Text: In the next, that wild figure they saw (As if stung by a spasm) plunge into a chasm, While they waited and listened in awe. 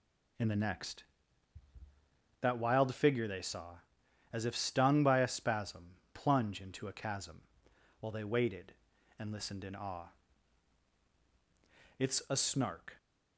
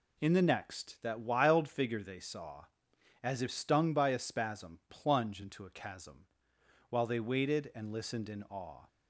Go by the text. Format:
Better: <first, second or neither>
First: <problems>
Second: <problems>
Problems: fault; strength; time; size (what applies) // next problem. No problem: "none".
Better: second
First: goes on to say "It's a Snark"; noticeable; from 11.9 s on; 0.98 s long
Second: none